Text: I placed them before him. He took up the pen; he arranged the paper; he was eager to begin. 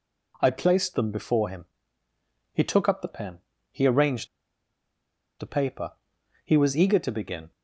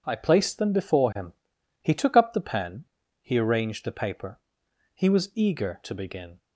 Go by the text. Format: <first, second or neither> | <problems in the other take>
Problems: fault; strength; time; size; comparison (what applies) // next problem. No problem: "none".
second | pauses between "arranged" and "the"; at 4.2 s; 1.1 s long